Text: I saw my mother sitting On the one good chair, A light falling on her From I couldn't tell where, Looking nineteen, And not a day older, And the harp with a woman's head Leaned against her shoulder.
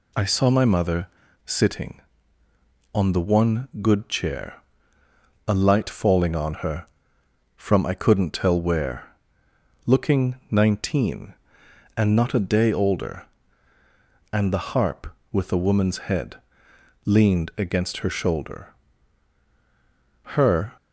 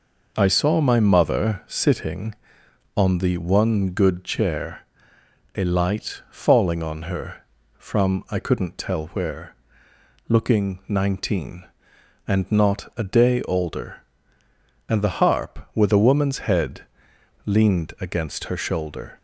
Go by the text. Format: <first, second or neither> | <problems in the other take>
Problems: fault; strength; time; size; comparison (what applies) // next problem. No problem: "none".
second | pauses between "mother" and "sitting"; at 1.0 s; 0.39 s long // pauses between "head" and "Leaned"; noticeable; at 16.3 s; 0.70 s long; noticeable in the second // goes on to say "Her"; slight; from 20.3 s on; 0.38 s long